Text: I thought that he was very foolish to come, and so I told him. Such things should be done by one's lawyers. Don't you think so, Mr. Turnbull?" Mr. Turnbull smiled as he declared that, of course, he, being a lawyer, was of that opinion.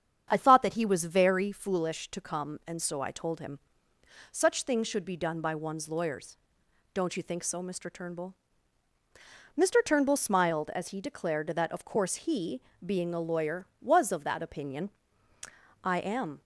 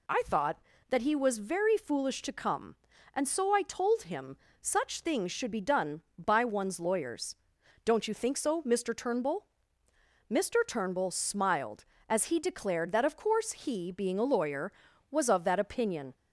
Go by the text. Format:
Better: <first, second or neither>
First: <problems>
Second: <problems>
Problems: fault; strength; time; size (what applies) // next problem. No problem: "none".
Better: second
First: starts louder than the rest; strong; until 1.3 s; 8 dB // goes on to say "I am"; from 15.8 s on; 0.60 s long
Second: none